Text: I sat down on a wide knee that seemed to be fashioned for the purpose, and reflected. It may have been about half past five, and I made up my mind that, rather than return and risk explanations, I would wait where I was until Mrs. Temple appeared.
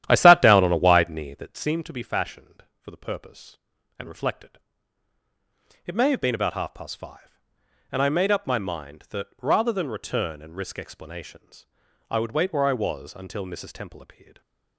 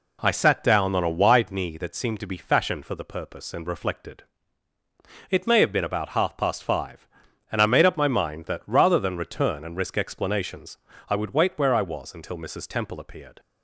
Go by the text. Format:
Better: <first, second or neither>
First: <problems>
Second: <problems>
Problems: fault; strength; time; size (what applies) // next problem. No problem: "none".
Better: second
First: starts louder than the rest; strong; until 1.8 s; 11.5 dB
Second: none